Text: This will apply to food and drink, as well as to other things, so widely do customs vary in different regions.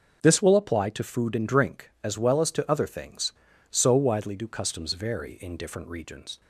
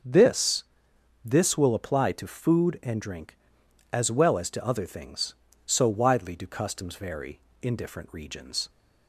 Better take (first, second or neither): first